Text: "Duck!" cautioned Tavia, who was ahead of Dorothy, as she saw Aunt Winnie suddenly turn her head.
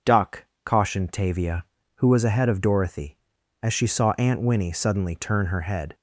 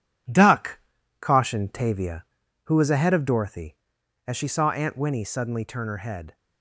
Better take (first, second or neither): first